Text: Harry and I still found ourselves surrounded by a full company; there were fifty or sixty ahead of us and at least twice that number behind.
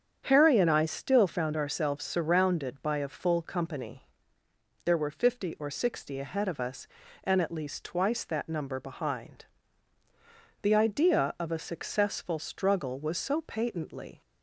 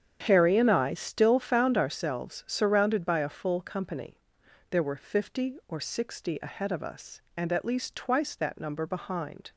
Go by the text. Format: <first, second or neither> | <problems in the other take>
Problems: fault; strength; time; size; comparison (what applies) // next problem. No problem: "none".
second | starts louder than the rest; strong; until 1.2 s; 8 dB; strong in the second // goes on to say "The idea of a successful struggle was so patently"; strong; from 10.6 s on; 3.6 s long